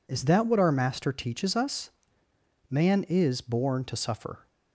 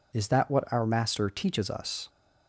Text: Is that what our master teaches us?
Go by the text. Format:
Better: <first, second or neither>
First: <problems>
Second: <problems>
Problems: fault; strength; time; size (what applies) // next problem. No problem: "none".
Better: second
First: goes on to say "Man is born to suffer"; strong; from 2.7 s on; 1.7 s long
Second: none